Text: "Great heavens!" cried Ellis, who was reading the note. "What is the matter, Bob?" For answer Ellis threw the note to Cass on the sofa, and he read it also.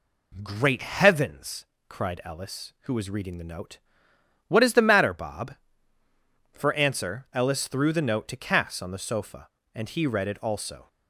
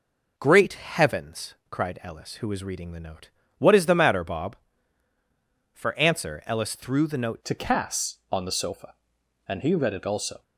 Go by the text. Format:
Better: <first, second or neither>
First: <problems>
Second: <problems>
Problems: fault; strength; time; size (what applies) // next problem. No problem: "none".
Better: first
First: none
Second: changes voice at "to"; from 7.4 s on; 3.0 s long